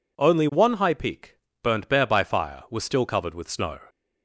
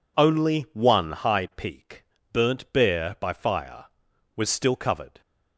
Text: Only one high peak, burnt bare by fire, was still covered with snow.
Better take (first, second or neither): first